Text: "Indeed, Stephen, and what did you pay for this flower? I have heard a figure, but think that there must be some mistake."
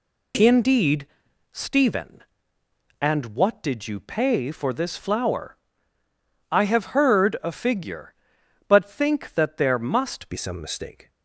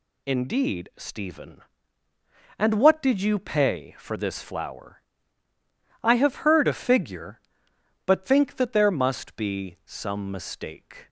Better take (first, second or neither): second